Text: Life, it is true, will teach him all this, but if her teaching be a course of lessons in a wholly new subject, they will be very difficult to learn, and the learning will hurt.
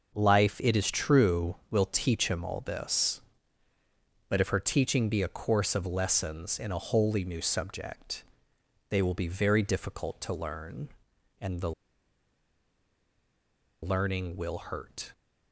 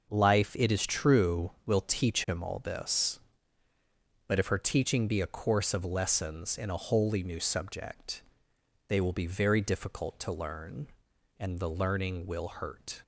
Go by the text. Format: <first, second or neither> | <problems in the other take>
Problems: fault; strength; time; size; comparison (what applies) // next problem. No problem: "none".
second | starts louder than the rest; until 1.1 s; 6.5 dB; also in the second // pauses between "the" and "learning"; strong; at 11.7 s; 2.1 s long